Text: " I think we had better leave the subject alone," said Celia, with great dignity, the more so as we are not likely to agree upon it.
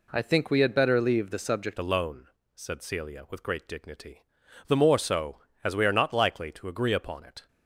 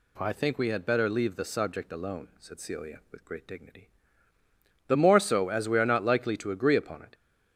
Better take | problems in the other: second | changes voice at "alone"; from 1.7 s on; 5.7 s long

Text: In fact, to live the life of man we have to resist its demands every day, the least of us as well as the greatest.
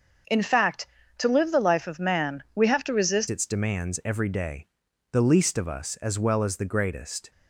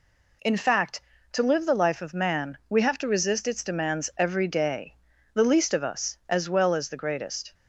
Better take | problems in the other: second | starts louder than the rest; until 1.5 s; 6.5 dB // changes voice at "its"; from 3.3 s on; 4.0 s long

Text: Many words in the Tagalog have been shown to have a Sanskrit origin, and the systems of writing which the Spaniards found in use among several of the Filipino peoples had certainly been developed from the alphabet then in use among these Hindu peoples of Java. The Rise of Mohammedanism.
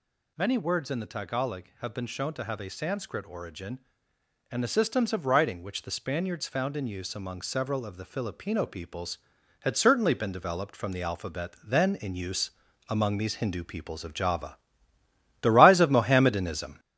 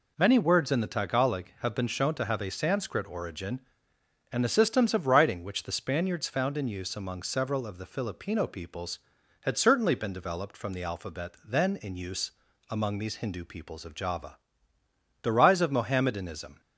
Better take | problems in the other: second | gets louder; noticeable; throughout; 4.5 dB // pauses between "use" and "among"; at 12.4 s; 0.40 s long; also in the second

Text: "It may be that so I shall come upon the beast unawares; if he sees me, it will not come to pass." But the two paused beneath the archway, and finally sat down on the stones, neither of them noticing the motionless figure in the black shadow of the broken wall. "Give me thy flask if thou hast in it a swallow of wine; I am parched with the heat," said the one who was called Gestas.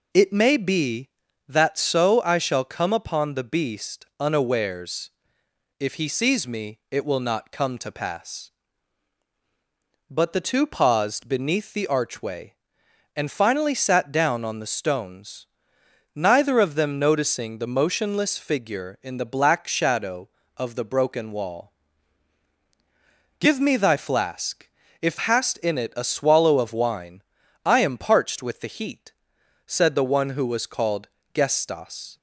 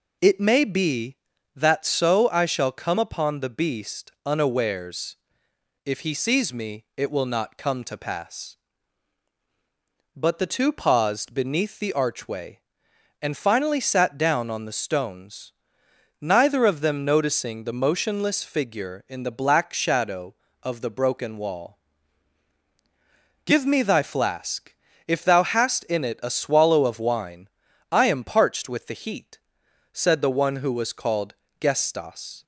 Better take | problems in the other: second | pauses between "flask" and "if"; slight; at 24.6 s; 0.32 s long; slight in the second // skips "thou"; at 25.1 s // pauses between "called" and "Gestas"; slight; at 31.0 s; 0.26 s long; slight in the second

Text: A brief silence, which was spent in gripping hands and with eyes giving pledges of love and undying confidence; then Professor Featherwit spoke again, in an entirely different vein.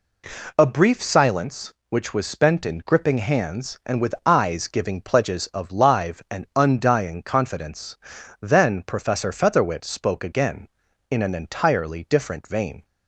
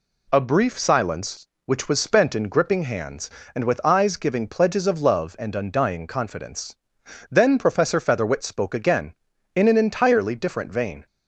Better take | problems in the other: second | says "live" for "love"; at 5.7 s

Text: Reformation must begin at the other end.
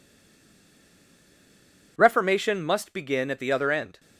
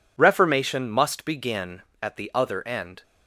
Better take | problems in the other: second | stays silent before the first word; noticeable; until 1.9 s; 1.9 s long

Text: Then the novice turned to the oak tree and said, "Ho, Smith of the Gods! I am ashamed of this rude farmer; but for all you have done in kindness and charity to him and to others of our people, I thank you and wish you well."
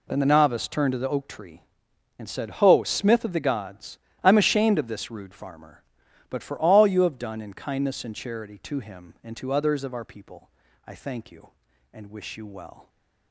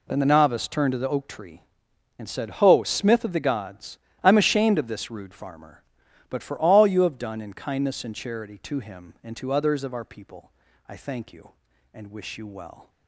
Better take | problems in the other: neither | none

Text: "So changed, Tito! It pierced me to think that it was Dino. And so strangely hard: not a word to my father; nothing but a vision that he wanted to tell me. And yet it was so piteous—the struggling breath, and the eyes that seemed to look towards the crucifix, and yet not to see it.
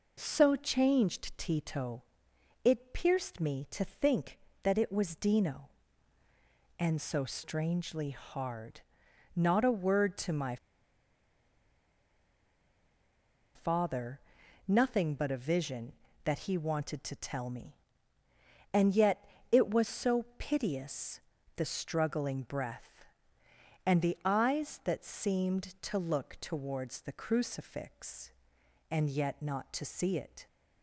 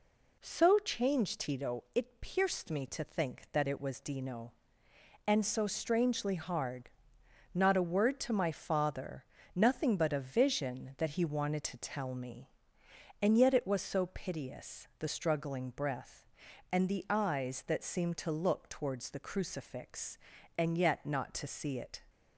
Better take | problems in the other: second | pauses between "my" and "father"; strong; at 10.5 s; 2.9 s long // pauses between "yet" and "it"; slight; at 19.2 s; 0.24 s long

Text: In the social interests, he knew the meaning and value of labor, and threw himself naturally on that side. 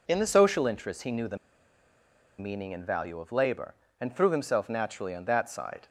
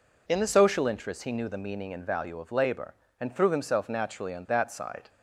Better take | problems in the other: second | pauses between "the" and "meaning"; at 1.3 s; 1.0 s long

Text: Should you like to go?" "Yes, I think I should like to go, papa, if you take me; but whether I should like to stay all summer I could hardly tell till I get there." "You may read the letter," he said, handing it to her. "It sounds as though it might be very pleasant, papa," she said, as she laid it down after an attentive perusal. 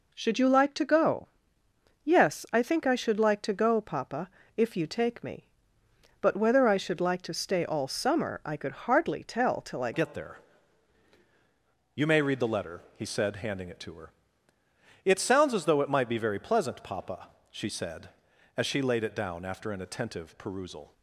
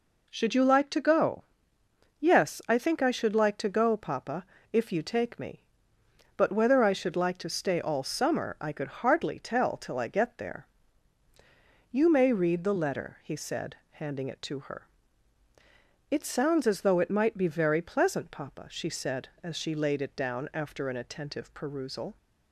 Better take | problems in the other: second | changes voice at "get"; from 9.9 s on; 11.0 s long

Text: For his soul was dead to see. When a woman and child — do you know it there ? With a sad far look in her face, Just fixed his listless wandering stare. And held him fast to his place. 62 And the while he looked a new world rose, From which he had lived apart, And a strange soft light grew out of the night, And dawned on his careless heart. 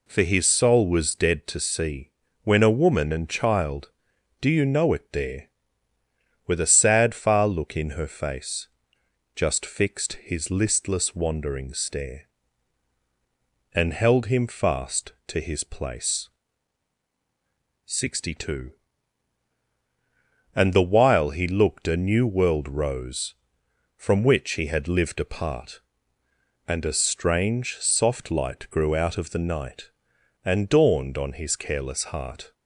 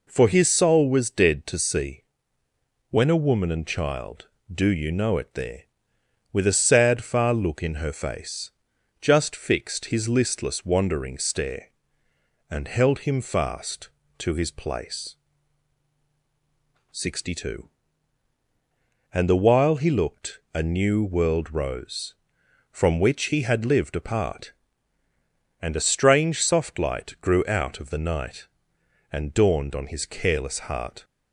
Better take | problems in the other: neither | none

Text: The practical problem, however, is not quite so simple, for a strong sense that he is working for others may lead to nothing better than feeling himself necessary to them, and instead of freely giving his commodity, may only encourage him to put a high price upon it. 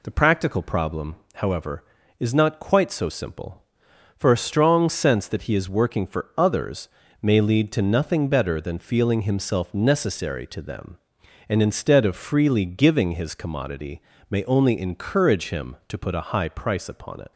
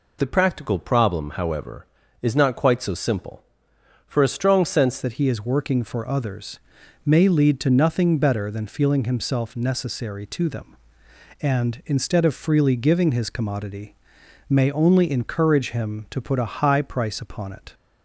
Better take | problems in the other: first | changes voice at "that"; from 5.0 s on; 12.7 s long // pauses between "others" and "may"; noticeable; at 6.5 s; 0.48 s long; slight in the first

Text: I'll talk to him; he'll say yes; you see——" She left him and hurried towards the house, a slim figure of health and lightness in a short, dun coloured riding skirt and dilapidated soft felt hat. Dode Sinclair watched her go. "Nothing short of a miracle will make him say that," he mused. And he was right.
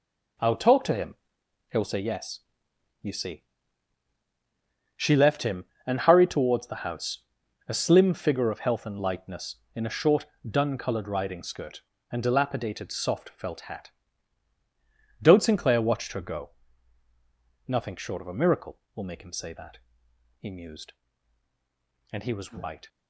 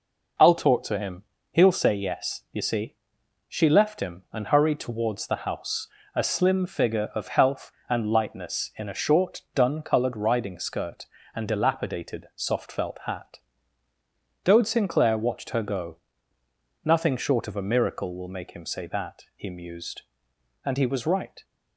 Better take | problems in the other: second | gets quieter; strong; throughout; 10 dB

